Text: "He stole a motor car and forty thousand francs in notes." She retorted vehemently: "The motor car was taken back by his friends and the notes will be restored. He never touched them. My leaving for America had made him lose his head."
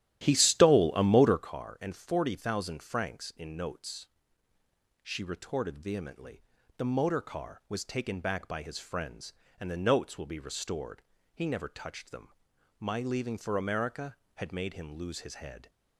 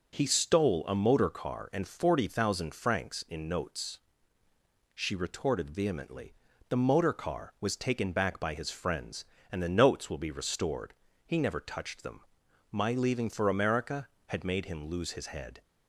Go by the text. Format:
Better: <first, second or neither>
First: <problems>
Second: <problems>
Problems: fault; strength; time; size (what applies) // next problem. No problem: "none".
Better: second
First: starts louder than the rest; strong; until 1.5 s; 12.5 dB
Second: none